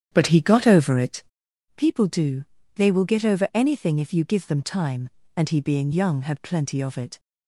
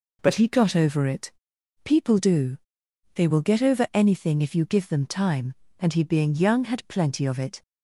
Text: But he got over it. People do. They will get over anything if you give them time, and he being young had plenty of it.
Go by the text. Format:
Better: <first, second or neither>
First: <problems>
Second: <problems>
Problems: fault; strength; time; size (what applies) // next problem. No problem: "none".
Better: second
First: starts louder than the rest; strong; until 1.7 s; 9.5 dB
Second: none